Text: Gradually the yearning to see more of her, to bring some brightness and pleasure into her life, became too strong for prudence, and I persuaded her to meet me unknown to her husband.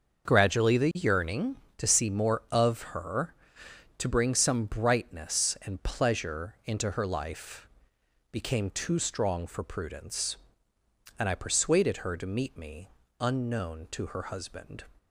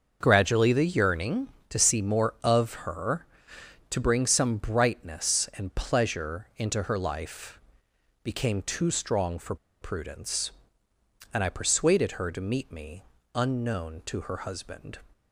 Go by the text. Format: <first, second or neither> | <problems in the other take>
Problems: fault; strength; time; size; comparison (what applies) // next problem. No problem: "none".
first | starts louder than the rest; until 1.2 s; 6.5 dB; also in the first // pauses between "for" and "prudence"; slight; at 9.5 s; 0.25 s long // pauses between "me" and "unknown"; slight; at 13.0 s; 0.30 s long; slight in the first